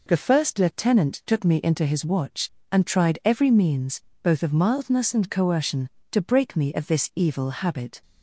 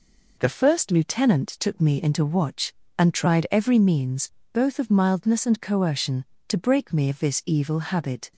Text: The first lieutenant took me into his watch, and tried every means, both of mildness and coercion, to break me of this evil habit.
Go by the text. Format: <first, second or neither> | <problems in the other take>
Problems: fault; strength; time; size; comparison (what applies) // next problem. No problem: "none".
first | skips "his"; at 2.2 s